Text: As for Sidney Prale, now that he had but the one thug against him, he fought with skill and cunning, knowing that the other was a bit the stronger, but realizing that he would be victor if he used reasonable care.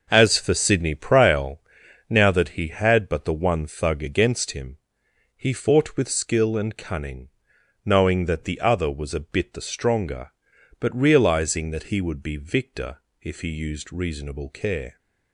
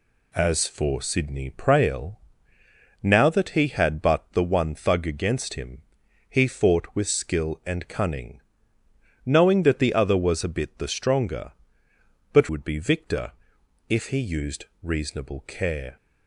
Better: first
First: pauses between "victor" and "if"; slight; at 12.9 s; 0.22 s long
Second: skips "realizing that he"; at 12.4 s // pauses between "victor" and "if"; noticeable; at 13.3 s; 0.58 s long // pauses between "used" and "reasonable"; slight; at 14.6 s; 0.16 s long

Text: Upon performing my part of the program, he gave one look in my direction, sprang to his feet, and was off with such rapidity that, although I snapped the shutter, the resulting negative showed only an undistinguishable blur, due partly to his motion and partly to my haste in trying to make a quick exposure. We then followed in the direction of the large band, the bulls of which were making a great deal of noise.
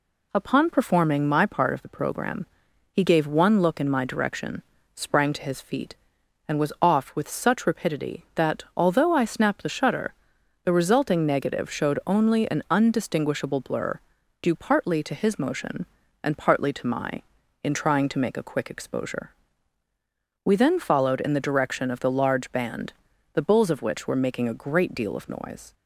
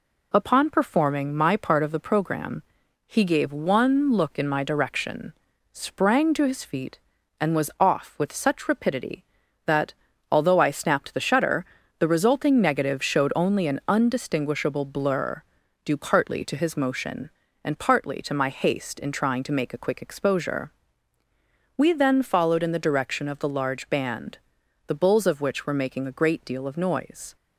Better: second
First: skips "haste"; at 17.4 s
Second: none

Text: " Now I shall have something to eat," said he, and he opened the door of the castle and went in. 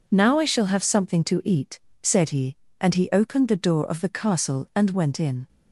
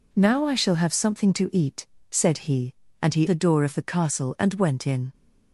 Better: first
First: none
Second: skips "opened"; at 3.2 s

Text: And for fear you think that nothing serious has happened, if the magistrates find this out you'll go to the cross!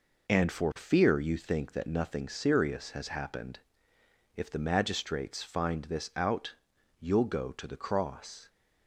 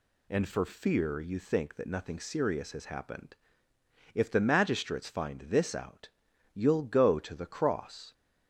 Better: neither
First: pauses between "out" and "you'll"; at 6.5 s; 0.42 s long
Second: pauses between "out" and "you'll"; at 6.0 s; 0.45 s long

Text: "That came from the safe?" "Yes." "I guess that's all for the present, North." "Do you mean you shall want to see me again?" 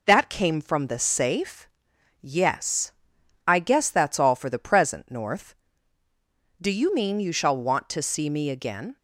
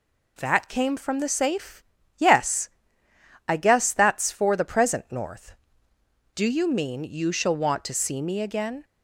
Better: first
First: none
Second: skips "all"; at 4.3 s

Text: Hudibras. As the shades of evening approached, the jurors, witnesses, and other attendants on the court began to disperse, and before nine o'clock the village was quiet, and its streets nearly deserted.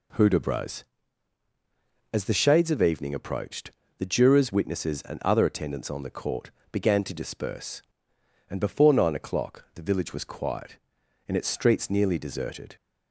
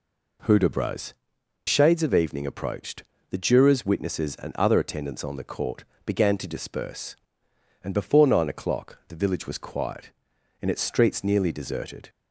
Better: first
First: pauses between "court" and "began"; slight; at 6.4 s; 0.22 s long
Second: skips "As the"; at 1.3 s // pauses between "court" and "began"; slight; at 5.8 s; 0.22 s long

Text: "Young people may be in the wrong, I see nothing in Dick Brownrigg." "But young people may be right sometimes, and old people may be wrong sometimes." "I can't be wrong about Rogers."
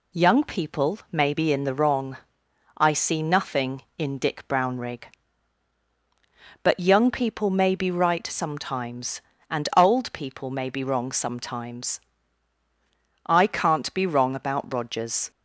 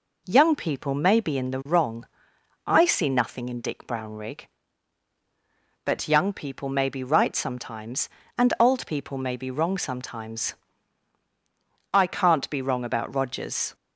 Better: neither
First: none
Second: none

